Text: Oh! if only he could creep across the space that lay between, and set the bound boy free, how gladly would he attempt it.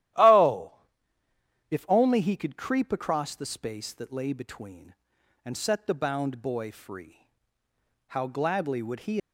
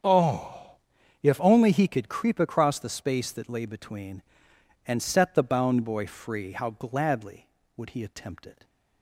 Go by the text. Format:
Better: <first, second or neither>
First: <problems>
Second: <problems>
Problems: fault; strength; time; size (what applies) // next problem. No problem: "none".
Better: second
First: starts louder than the rest; strong; until 2.2 s; 13 dB // stops before "attempt it"; at 9.1 s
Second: starts louder than the rest; strong; until 1.7 s; 8 dB